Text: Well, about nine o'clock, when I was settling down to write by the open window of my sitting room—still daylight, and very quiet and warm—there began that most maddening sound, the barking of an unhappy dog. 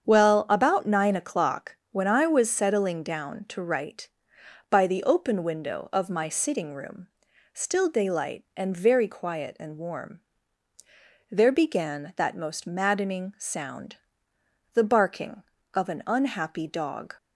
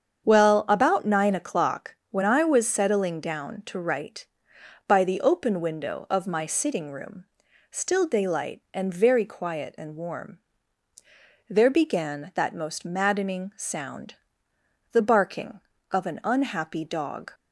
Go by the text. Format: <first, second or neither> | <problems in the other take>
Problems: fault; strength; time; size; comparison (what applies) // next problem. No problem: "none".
neither | starts louder than the rest; strong; the same in both